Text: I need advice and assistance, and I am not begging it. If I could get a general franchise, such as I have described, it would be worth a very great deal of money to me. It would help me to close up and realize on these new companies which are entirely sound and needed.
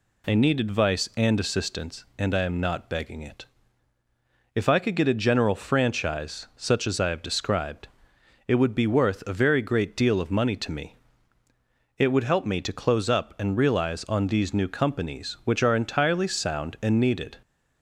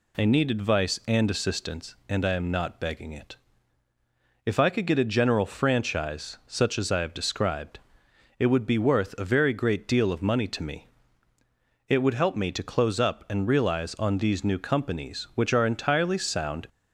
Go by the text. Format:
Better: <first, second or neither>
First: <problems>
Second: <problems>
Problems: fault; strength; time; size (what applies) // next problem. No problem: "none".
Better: first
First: none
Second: stops before "and needed"; at 16.6 s